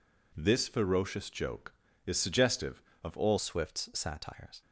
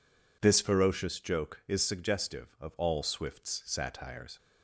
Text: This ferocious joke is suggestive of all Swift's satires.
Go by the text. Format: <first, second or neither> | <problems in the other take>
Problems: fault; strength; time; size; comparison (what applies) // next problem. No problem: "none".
second | changes voice at "Swift's"; from 3.3 s on; 1.3 s long